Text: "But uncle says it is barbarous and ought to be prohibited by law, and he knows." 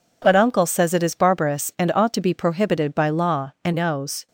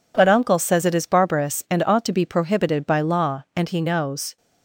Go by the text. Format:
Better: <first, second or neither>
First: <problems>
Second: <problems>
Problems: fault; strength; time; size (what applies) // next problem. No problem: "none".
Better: second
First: skips "he"; at 3.7 s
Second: none